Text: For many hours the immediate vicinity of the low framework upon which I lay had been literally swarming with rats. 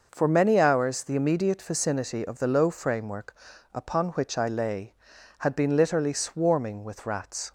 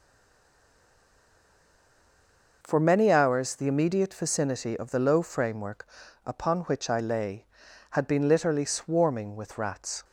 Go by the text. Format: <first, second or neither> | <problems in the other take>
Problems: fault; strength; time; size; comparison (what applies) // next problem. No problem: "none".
first | stays silent before the first word; strong; until 2.6 s; 2.6 s long // pauses between "framework" and "upon"; at 5.8 s; 0.38 s long; also in the first